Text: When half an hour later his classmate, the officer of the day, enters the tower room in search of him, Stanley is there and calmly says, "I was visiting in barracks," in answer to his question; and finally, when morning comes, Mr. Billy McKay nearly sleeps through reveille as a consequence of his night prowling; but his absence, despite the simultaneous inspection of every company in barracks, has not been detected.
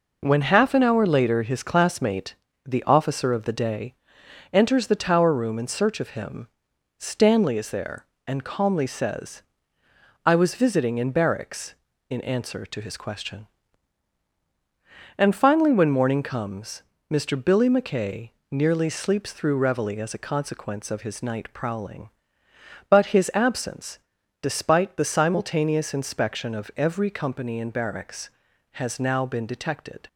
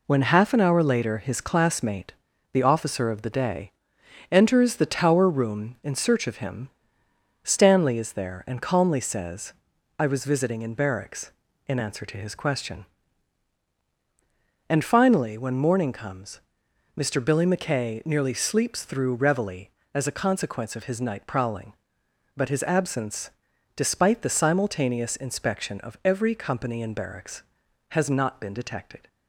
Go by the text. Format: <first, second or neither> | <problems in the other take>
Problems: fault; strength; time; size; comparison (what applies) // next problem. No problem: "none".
second | pauses between "McKay" and "nearly"; slight; at 18.2 s; 0.20 s long // says "now" for "not"; at 29.0 s